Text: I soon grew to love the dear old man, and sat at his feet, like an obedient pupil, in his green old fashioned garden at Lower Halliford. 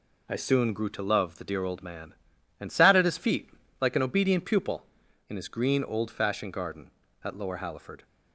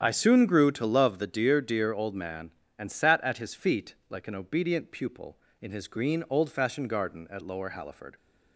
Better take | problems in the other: first | starts louder than the rest; strong; until 1.0 s; 8.5 dB // says "dear" twice; at 1.6 s

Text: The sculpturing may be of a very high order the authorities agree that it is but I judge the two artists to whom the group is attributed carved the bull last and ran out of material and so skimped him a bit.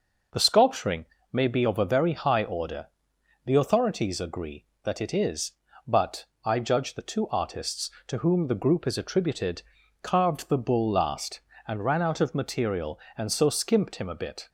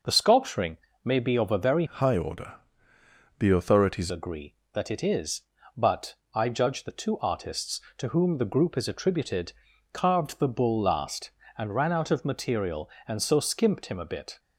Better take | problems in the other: first | pauses between "sculpturing" and "may"; slight; at 0.7 s; 0.26 s long; slight in the first // changes voice from "high" to "authorities"; from 1.8 to 4.1 s; 2.3 s long // pauses between "order" and "the"; noticeable; at 2.5 s; 0.84 s long; noticeable in the first // pauses between "but" and "I"; slight; at 6.1 s; 0.18 s long; slight in the first // pauses between "attributed" and "carved"; at 9.5 s; 0.40 s long; also in the first

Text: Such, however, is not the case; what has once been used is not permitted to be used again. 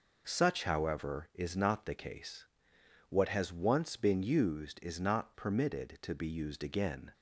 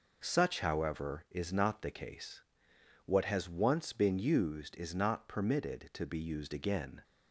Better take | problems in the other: neither | none

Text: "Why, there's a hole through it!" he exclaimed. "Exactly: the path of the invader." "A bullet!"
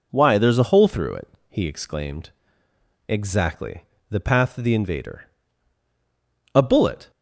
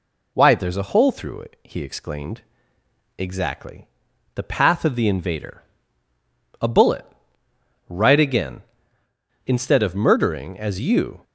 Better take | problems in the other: first | goes on to say "Right again Instead of murdering as you"; strong; from 7.8 s on; 3.3 s long

